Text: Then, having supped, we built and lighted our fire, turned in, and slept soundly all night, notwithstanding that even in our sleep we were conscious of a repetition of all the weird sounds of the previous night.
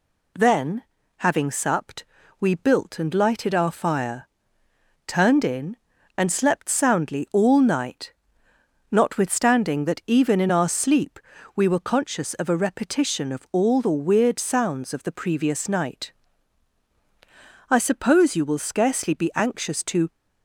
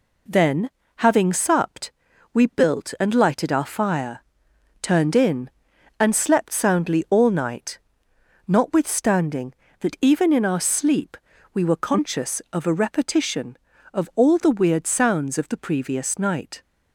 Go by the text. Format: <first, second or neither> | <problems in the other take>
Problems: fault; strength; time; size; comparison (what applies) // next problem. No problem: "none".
second | pauses between "sleep" and "we"; slight; at 11.1 s; 0.36 s long; slight in the second // goes on to say "I suppose you will scarcely be anxious to"; strong; from 17.6 s on; 2.4 s long